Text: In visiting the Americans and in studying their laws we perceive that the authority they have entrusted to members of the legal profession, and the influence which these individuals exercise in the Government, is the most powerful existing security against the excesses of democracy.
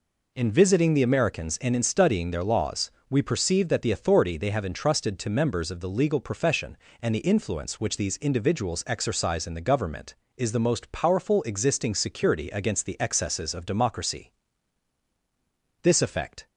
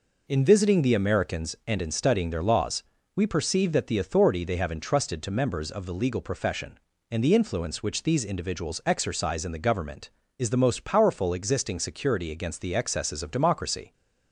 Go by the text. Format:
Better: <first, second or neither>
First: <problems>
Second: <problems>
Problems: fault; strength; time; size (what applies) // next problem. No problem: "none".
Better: second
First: pauses between "laws" and "we"; slight; at 2.8 s; 0.22 s long // goes on to say "This effect"; noticeable; from 15.8 s on; 0.64 s long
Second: pauses between "laws" and "we"; slight; at 2.8 s; 0.32 s long